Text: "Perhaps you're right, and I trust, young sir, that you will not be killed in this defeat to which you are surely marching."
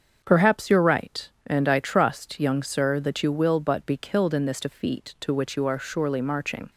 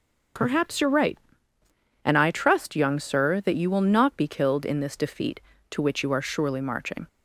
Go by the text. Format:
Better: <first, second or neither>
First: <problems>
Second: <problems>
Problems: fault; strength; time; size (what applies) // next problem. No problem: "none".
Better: second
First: starts louder than the rest; until 1.2 s; 7 dB // says "but" for "not"; at 3.5 s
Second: starts louder than the rest; until 2.2 s; 6.5 dB